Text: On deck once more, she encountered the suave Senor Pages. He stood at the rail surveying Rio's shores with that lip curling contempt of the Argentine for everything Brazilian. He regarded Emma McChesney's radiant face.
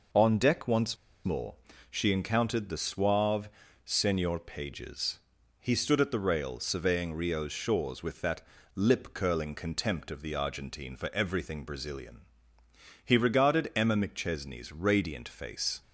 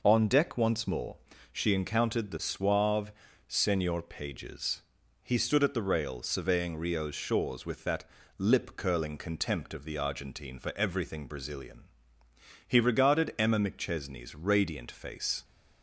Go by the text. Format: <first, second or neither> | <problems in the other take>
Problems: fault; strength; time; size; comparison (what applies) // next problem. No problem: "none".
second | pauses between "once" and "more"; slight; at 0.9 s; 0.28 s long // pauses between "suave" and "Senor"; slight; at 3.4 s; 0.36 s long; slight in the second // pauses between "that" and "lip"; slight; at 8.4 s; 0.30 s long; slight in the second